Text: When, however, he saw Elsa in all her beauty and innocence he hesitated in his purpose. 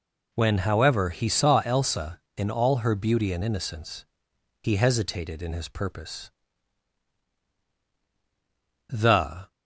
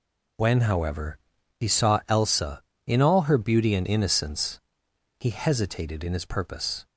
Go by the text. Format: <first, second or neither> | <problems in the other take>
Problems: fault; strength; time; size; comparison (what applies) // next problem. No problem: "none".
second | pauses between "innocence" and "he"; noticeable; at 4.0 s; 0.58 s long; noticeable in the second // goes on to say "The"; noticeable; from 8.8 s on; 0.64 s long